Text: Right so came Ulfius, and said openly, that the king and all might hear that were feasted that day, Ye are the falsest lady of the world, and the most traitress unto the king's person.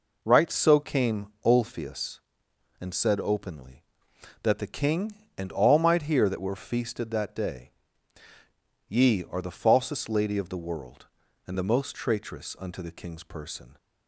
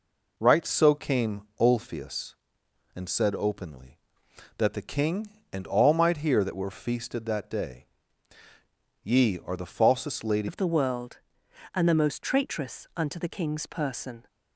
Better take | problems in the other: first | changes voice at "of"; from 10.4 s on; 3.8 s long

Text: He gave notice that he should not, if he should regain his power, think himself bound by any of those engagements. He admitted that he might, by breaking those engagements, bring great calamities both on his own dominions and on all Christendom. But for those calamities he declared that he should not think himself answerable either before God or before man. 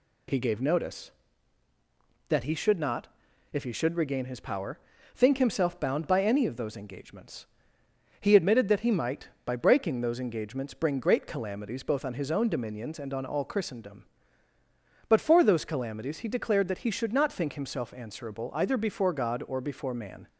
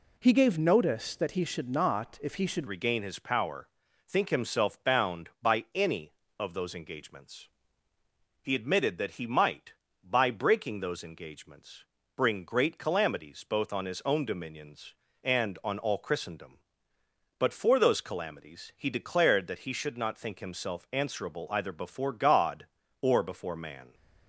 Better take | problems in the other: first | changes voice at "regain"; from 2.6 s on; 21.3 s long

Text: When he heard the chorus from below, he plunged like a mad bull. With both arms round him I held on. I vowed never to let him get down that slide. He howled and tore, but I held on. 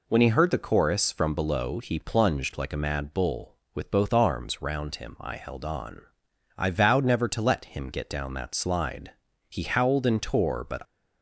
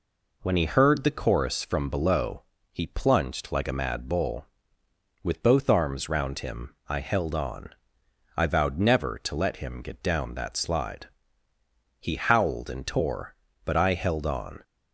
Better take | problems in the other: second | stops before "I held on"; at 10.8 s

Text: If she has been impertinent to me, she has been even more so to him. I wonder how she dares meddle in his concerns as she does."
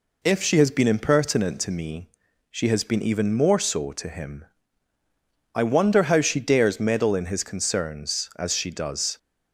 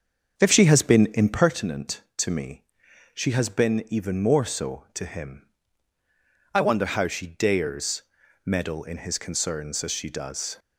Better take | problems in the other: first | starts louder than the rest; strong; until 1.5 s; 7 dB // pauses between "dares" and "meddle"; at 8.0 s; 0.42 s long

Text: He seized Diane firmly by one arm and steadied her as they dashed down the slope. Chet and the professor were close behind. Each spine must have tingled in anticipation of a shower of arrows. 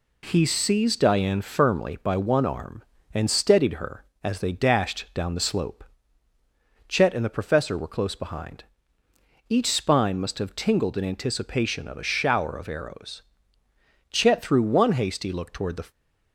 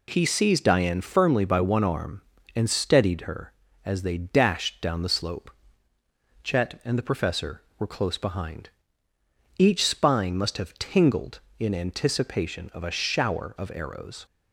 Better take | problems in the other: second | goes on to say "Chet threw one hasty look toward the"; strong; from 14.0 s on; 1.8 s long

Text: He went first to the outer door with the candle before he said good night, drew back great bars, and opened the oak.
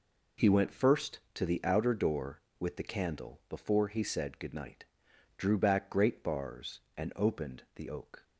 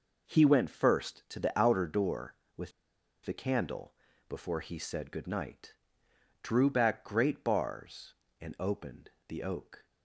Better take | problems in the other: first | pauses between "with" and "the"; noticeable; at 2.7 s; 0.54 s long // pauses between "candle" and "before"; slight; at 3.9 s; 0.34 s long // pauses between "opened" and "the"; slight; at 9.0 s; 0.18 s long

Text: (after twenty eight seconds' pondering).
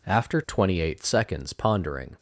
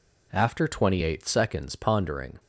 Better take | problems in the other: neither | none

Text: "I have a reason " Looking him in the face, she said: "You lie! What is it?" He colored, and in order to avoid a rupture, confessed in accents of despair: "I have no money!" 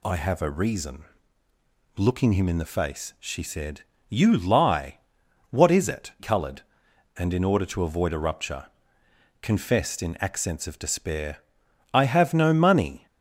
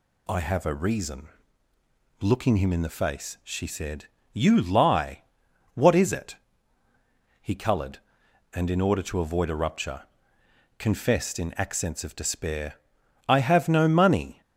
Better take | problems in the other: second | skips "He"; at 6.1 s

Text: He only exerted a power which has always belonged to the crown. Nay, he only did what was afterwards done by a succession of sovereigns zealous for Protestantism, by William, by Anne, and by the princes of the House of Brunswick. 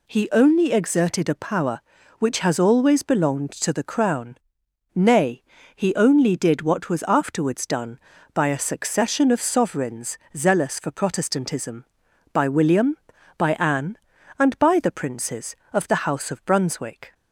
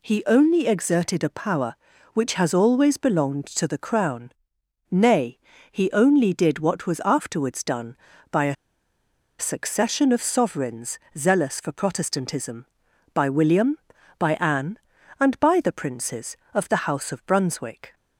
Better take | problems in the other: first | pauses between "a" and "succession"; noticeable; at 8.5 s; 0.83 s long // pauses between "sovereigns" and "zealous"; slight; at 10.9 s; 0.18 s long; slight in the first

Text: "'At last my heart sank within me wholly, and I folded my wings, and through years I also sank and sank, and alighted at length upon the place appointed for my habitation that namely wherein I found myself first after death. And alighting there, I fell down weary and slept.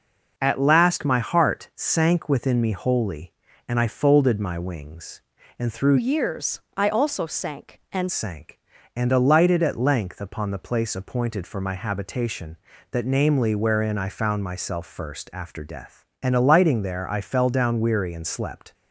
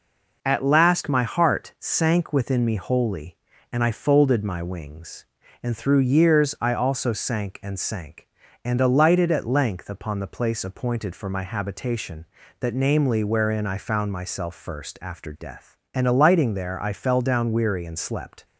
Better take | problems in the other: second | changes voice from "years" to "and"; from 5.9 to 8.0 s; 2.1 s long // pauses between "years" and "I"; slight; at 6.5 s; 0.16 s long

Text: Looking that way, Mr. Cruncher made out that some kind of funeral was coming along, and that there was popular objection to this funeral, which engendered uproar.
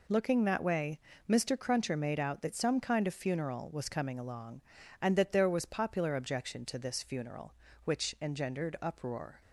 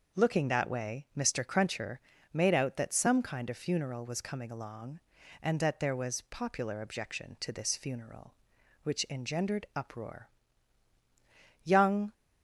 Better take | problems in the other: first | pauses between "Cruncher" and "made"; slight; at 1.9 s; 0.36 s long // goes on to say "Young"; from 11.6 s on; 0.50 s long

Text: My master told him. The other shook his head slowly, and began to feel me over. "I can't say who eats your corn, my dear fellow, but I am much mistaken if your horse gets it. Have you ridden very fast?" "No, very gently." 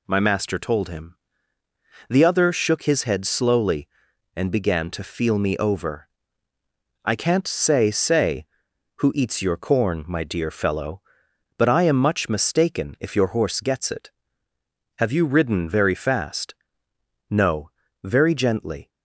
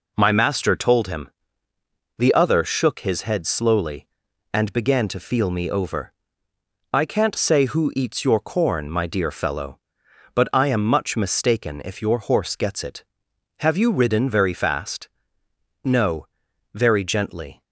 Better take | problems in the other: second | says "say" twice; at 7.9 s

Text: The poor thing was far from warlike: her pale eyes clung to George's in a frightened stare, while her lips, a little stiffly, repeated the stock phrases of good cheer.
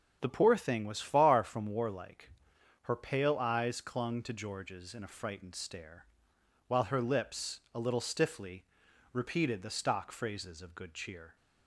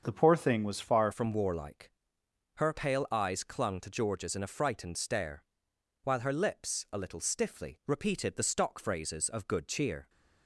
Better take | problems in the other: first | starts louder than the rest; until 1.0 s; 7 dB; also in the first // changes voice at "from"; from 1.1 s on; 8.9 s long

